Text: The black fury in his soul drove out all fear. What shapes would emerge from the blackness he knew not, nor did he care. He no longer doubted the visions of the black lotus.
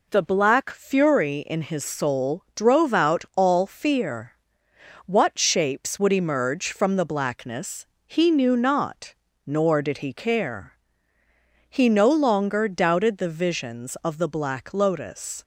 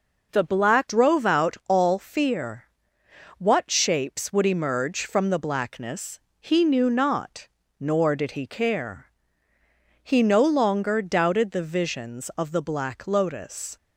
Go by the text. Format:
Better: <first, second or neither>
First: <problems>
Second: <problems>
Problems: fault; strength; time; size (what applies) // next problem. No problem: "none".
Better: first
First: pauses between "blackness" and "he"; slight; at 7.8 s; 0.20 s long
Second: skips "fury in his soul"; at 0.8 s // pauses between "blackness" and "he"; slight; at 6.1 s; 0.20 s long